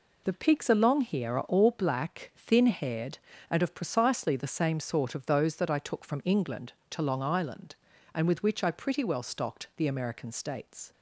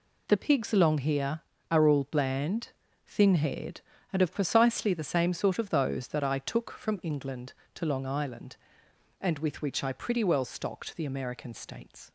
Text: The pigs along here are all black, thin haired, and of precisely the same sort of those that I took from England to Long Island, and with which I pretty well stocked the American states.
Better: first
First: none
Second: says "bland" for "black"; at 2.0 s

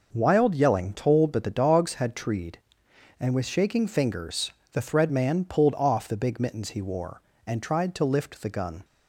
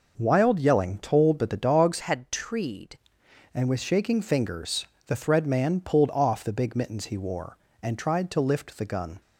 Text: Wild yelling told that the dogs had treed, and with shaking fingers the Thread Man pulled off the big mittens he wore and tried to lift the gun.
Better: first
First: pauses between "fingers" and "the"; slight; at 4.4 s; 0.22 s long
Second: changes voice from "had" to "treed"; from 2.0 to 2.9 s; 0.9 s long // pauses between "fingers" and "the"; slight; at 4.8 s; 0.22 s long

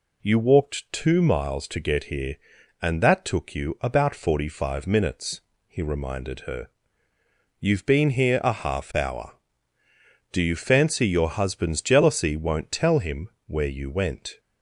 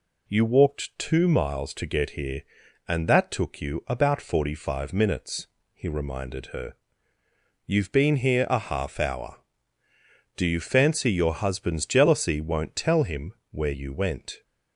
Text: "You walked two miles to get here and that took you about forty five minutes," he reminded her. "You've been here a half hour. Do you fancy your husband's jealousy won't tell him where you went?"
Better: neither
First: pauses between "him" and "where"; slight; at 13.2 s; 0.16 s long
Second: pauses between "him" and "where"; slight; at 13.3 s; 0.16 s long

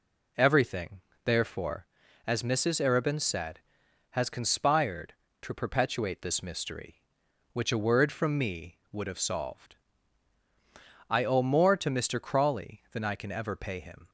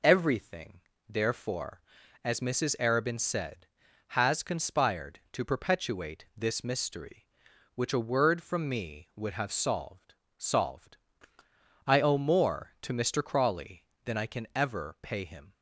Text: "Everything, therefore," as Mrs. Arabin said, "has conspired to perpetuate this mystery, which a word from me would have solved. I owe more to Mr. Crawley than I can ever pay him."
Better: first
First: none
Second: says "solved" twice; at 10.3 s

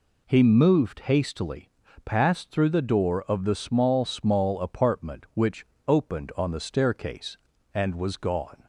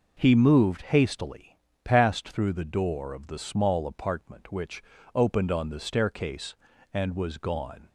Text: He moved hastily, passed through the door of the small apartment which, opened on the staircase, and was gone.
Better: second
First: says "small" twice; at 4.0 s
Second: none

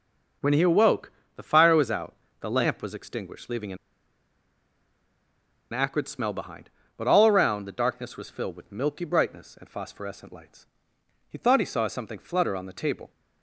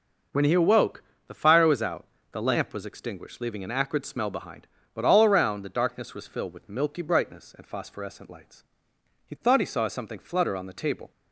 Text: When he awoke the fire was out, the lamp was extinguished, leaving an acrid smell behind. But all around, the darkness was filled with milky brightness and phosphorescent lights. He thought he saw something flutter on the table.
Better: second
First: pauses between "awoke" and "the"; slight; at 1.1 s; 0.24 s long // pauses between "an" and "acrid"; strong; at 3.7 s; 1.9 s long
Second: pauses between "awoke" and "the"; slight; at 1.0 s; 0.24 s long

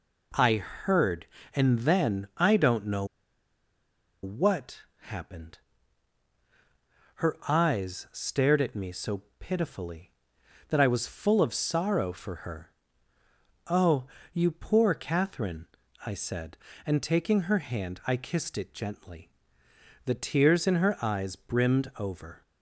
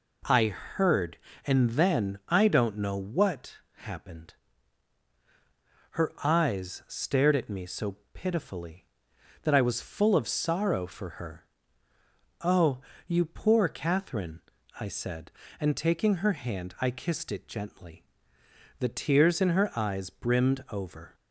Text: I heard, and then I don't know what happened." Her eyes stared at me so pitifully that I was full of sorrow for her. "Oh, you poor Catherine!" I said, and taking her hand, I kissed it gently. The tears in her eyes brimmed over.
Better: second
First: pauses between "know" and "what"; at 3.0 s; 1.1 s long // pauses between "what" and "happened"; slight; at 4.8 s; 0.16 s long // pauses between "so" and "pitifully"; slight; at 9.2 s; 0.16 s long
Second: pauses between "what" and "happened"; slight; at 3.5 s; 0.16 s long // pauses between "so" and "pitifully"; slight; at 7.9 s; 0.16 s long

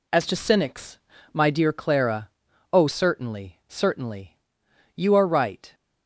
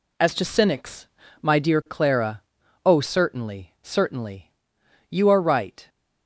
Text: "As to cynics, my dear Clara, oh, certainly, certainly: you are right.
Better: neither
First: none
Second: none

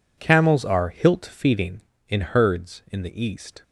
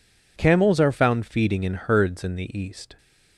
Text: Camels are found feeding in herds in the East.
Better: second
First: says "hilt" for "found"; at 0.8 s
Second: none

